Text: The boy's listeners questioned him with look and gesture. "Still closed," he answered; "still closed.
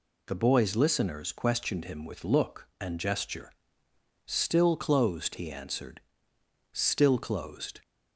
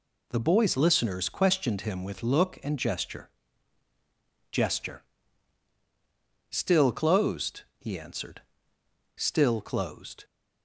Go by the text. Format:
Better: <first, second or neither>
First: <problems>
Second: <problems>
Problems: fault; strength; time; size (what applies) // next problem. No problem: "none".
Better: first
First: none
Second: says "gesture" twice; at 4.5 s